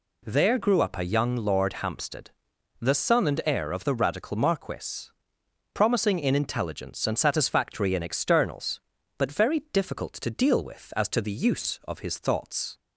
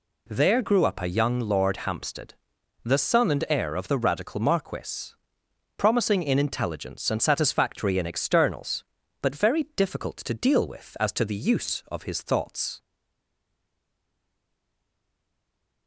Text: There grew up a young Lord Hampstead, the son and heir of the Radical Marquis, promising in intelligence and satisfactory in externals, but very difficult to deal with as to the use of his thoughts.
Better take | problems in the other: first | stays silent after the last word; strong; from 12.8 s on; 3.0 s long

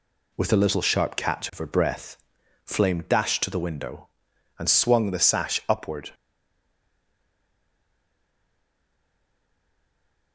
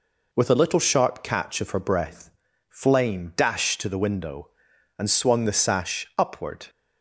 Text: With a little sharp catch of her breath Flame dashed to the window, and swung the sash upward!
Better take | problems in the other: second | pauses between "breath" and "Flame"; noticeable; at 2.1 s; 0.48 s long; also in the second // stays silent after the last word; strong; from 6.1 s on; 4.2 s long

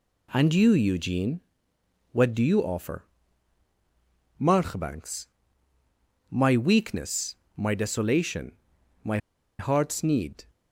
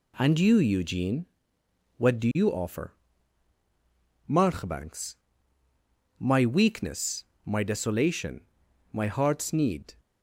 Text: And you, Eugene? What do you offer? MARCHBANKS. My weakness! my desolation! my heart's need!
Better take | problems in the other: second | pauses between "my" and "heart's"; at 9.1 s; 0.41 s long

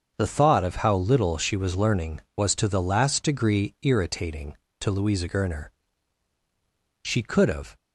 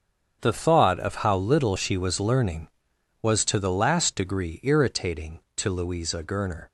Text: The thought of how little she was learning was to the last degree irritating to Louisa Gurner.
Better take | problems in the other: second | starts louder than the rest; until 1.1 s; 6.5 dB; strong in the second // goes on to say "She could have"; noticeable; from 7.0 s on; 0.74 s long

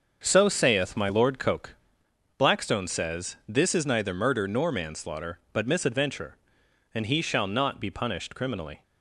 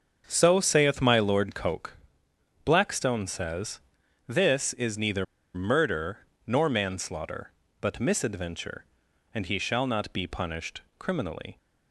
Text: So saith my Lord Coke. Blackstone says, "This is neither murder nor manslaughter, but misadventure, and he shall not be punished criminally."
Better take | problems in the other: first | starts louder than the rest; until 1.2 s; 6.5 dB; also in the first // pauses between "neither" and "murder"; slight; at 5.2 s; 0.30 s long // pauses between "murder" and "nor"; slight; at 6.1 s; 0.26 s long // pauses between "punished" and "criminally"; slight; at 10.8 s; 0.18 s long

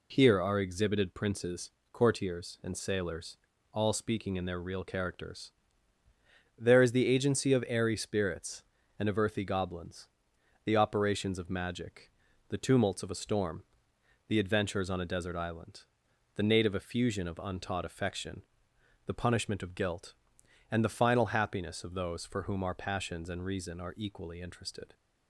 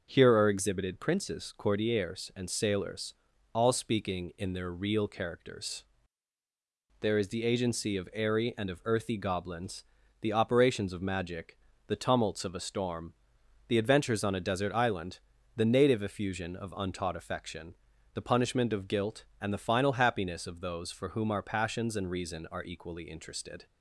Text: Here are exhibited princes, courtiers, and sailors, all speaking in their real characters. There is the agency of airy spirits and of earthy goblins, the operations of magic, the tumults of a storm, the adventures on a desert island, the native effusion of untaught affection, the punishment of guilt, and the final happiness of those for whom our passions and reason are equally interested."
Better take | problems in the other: first | starts louder than the rest; until 1.1 s; 6.5 dB // skips "spirits"; at 8.5 s

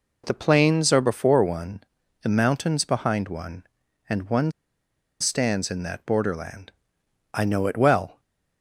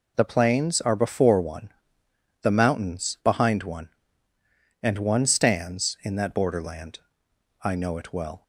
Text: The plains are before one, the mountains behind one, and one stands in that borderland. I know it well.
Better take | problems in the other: second | pauses between "one" and "stands"; noticeable; at 4.5 s; 0.69 s long

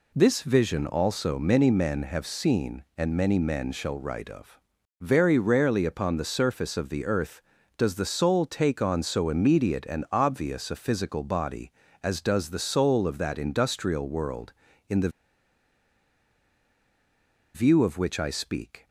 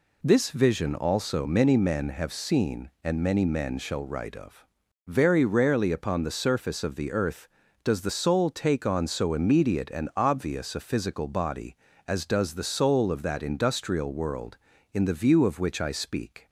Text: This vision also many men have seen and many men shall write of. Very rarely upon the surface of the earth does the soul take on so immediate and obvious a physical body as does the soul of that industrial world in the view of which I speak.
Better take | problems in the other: second | pauses between "the" and "view"; strong; at 15.0 s; 2.4 s long

